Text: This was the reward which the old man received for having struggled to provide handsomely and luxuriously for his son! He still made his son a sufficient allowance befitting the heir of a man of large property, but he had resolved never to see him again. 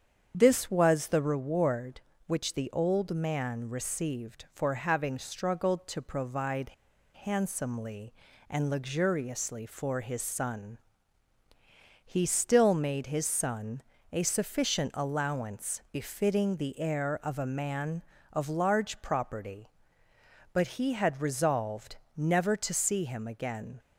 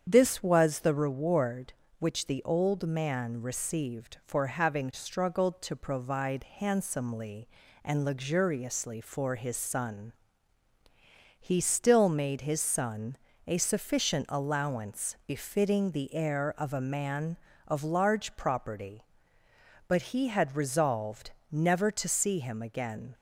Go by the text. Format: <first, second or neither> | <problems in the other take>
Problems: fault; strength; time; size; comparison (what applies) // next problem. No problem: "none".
second | starts louder than the rest; strong; until 1.3 s; 7.5 dB; strong in the second // pauses between "provide" and "handsomely"; noticeable; at 6.7 s; 0.51 s long // pauses between "son" and "a"; slight; at 13.8 s; 0.28 s long; slight in the second // pauses between "resolved" and "never"; slight; at 21.9 s; 0.22 s long; slight in the second